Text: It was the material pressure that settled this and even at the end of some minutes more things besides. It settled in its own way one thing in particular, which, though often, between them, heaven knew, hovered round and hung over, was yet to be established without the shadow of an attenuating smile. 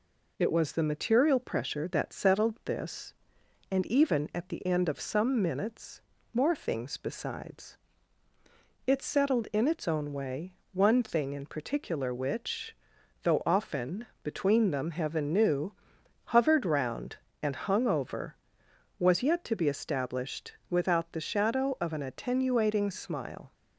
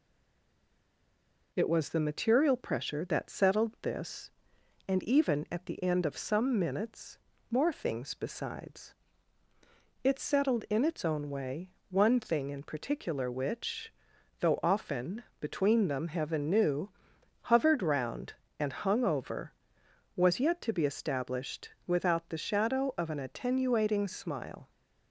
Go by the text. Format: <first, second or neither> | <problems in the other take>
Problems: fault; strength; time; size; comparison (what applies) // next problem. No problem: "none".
first | stays silent before the first word; noticeable; until 1.5 s; 1.5 s long // pauses between "minutes" and "more"; slight; at 7.1 s; 0.32 s long; slight in the first // pauses between "way" and "one"; slight; at 11.7 s; 0.20 s long; slight in the first